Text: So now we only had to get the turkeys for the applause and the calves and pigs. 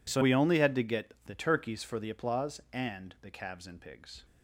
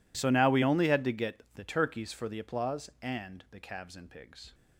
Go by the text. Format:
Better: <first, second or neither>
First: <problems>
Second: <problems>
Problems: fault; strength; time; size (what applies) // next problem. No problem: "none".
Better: second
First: skips "now"; at 0.2 s // pauses between "get" and "the"; slight; at 1.1 s; 0.16 s long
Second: pauses between "get" and "the"; slight; at 1.3 s; 0.16 s long